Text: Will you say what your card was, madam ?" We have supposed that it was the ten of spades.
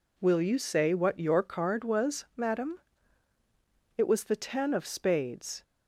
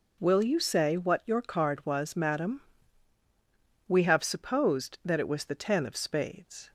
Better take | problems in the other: second | skips "We have supposed that"; at 3.9 s

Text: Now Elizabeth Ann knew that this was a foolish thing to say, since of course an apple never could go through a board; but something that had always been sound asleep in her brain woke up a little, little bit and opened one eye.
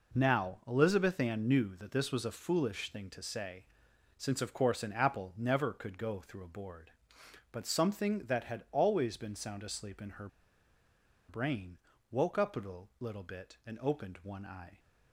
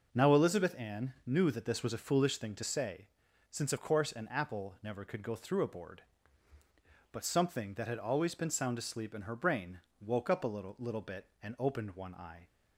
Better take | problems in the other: second | pauses between "her" and "brain"; at 10.2 s; 1.0 s long // pauses between "brain" and "woke"; slight; at 11.7 s; 0.34 s long; slight in the second

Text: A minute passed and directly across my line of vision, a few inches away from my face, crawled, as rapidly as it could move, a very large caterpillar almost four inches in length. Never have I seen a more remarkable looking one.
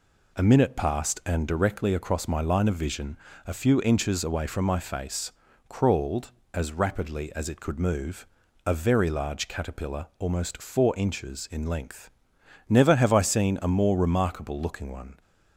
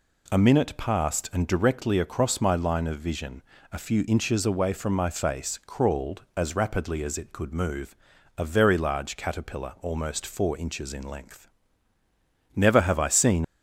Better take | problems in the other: first | stops before "a more remarkable looking one"; at 13.4 s

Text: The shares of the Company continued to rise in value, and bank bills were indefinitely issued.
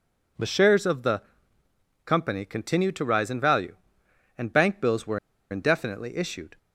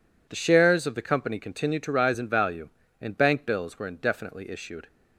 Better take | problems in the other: second | pauses between "the" and "Company"; noticeable; at 1.2 s; 0.82 s long // pauses between "were" and "indefinitely"; slight; at 5.1 s; 0.32 s long

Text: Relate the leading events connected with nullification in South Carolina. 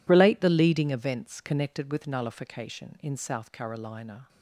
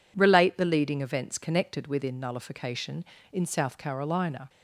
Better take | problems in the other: first | says "within" for "with"; at 1.8 s

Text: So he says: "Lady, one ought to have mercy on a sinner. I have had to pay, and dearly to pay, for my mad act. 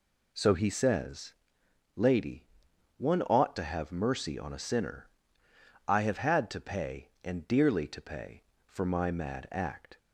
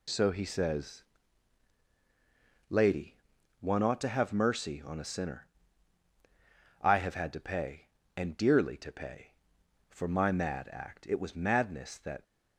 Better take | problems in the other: first | goes on to say "It was madness that"; noticeable; from 11.0 s on; 1.1 s long

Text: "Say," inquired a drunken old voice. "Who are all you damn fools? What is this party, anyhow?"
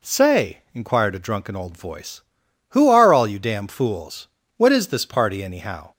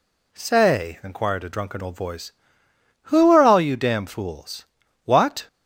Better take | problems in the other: first | stops before "is this party anyhow"; at 5.4 s

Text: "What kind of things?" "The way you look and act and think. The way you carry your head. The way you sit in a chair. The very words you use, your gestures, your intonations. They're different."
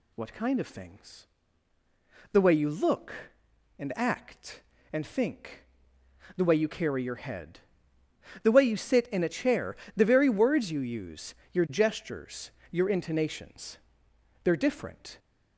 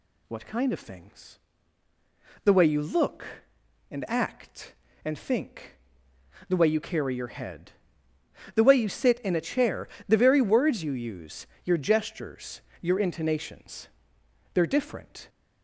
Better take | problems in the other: neither | none

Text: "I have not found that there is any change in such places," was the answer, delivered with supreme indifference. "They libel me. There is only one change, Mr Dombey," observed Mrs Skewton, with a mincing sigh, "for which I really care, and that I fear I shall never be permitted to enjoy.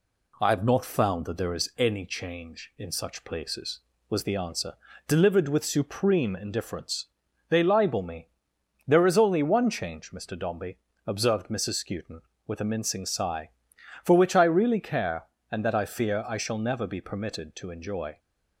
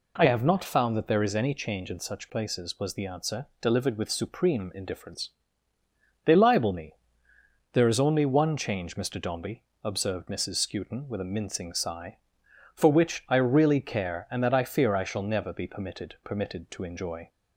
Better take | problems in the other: first | says "permitted" twice; at 16.2 s

